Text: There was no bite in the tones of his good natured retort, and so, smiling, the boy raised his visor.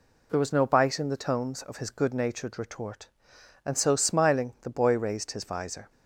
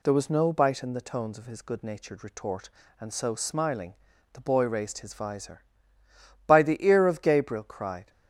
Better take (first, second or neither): first